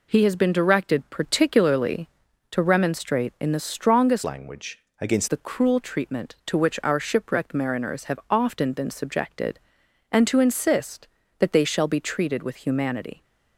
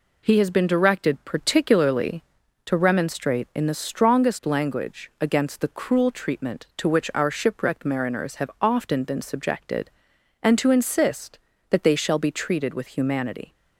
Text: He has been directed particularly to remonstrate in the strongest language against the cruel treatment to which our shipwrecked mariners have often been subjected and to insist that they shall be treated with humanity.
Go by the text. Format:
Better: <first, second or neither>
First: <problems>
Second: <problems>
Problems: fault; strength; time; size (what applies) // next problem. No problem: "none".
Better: second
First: changes voice from "language" to "against"; from 4.2 to 5.2 s; 1.0 s long // pauses between "language" and "against"; slight; at 4.7 s; 0.20 s long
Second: none